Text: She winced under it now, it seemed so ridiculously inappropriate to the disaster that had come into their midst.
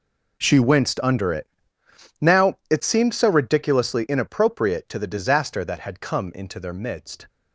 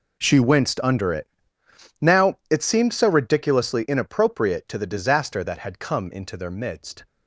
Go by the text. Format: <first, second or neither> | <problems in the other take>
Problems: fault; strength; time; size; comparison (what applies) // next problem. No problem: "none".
neither | pauses between "it" and "now"; noticeable; the same in both